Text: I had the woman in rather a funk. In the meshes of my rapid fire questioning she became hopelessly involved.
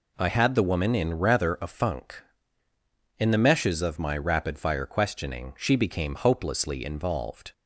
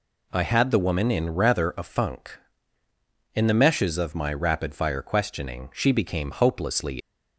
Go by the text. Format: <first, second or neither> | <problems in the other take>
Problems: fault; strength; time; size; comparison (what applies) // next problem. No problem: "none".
first | stops before "involved"; at 7.0 s